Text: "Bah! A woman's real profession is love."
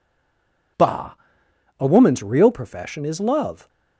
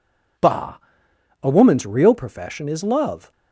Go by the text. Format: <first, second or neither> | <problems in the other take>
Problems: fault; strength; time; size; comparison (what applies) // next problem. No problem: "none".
second | stays silent before the first word; slight; until 0.7 s; 0.7 s long